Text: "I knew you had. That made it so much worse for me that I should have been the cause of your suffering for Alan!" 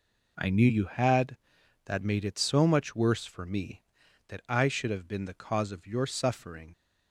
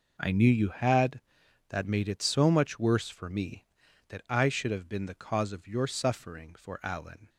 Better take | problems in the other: second | stops before "for Alan"; at 6.7 s

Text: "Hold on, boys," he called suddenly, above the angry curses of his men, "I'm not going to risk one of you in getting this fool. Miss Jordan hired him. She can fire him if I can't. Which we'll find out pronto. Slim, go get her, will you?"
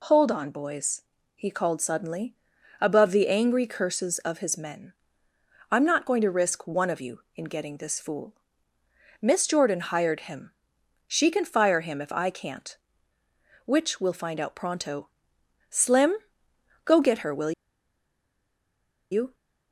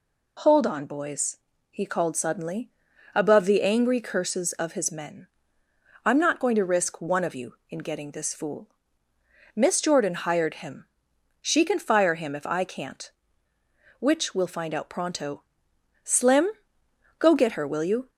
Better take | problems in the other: second | pauses between "will" and "you"; strong; at 17.5 s; 1.5 s long

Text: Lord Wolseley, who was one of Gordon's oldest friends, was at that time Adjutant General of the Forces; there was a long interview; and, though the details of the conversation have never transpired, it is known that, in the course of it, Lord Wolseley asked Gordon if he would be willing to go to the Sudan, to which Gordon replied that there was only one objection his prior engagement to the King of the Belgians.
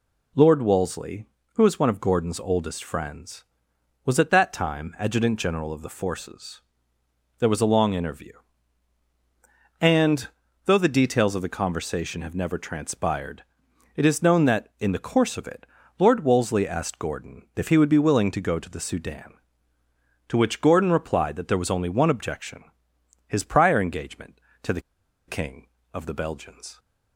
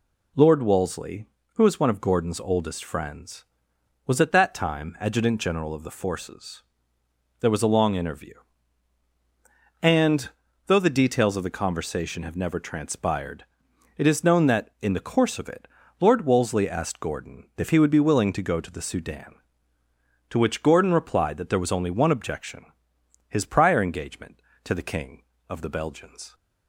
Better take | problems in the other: second | pauses between "objection" and "his"; noticeable; at 22.6 s; 0.64 s long; noticeable in the second // pauses between "the" and "King"; noticeable; at 24.8 s; 0.46 s long

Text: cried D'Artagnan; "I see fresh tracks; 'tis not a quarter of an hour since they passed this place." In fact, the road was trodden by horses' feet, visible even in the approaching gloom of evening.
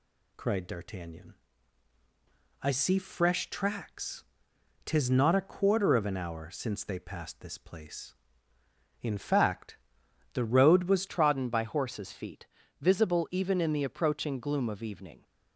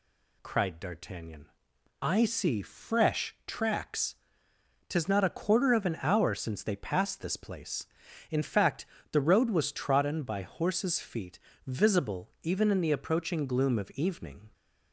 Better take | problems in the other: second | changes voice at "trodden"; from 11.0 s on; 4.2 s long

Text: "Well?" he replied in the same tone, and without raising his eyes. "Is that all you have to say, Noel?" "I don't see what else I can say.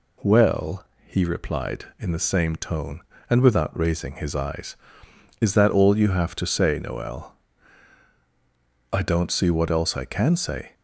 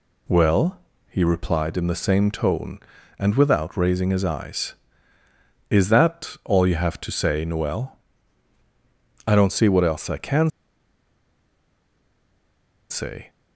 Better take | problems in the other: first | pauses between "can" and "say"; strong; at 10.4 s; 2.4 s long

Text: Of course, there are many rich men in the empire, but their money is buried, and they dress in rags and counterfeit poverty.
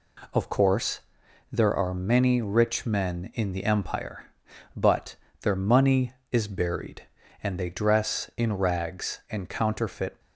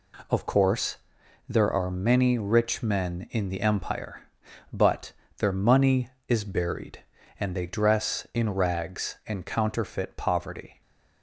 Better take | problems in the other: second | pauses between "but" and "their"; slight; at 5.1 s; 0.24 s long; slight in the second // stops before "poverty"; at 10.2 s

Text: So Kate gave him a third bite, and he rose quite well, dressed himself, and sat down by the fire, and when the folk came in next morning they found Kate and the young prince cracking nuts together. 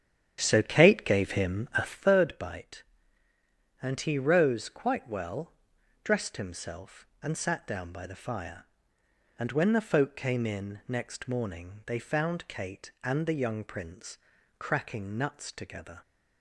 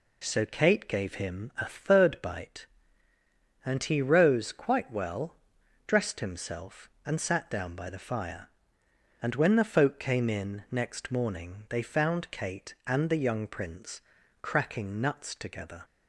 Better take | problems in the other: second | starts louder than the rest; strong; until 2.1 s; 9.5 dB // pauses between "prince" and "cracking"; at 14.1 s; 0.42 s long; also in the second

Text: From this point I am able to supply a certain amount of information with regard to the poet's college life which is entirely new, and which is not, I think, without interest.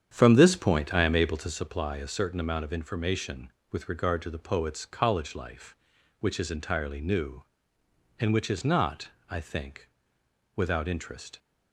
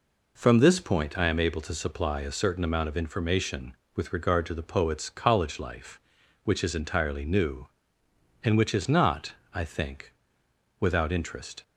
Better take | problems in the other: second | starts louder than the rest; strong; until 1.6 s; 8.5 dB

